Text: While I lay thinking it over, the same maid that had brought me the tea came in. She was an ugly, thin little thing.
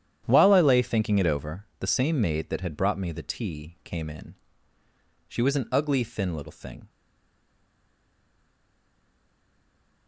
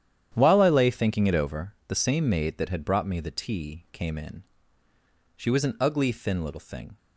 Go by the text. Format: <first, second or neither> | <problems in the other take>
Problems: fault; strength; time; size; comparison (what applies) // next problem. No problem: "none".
second | starts louder than the rest; strong; until 1.2 s; 10 dB; strong in the second // stays silent after the last word; strong; from 6.8 s on; 3.2 s long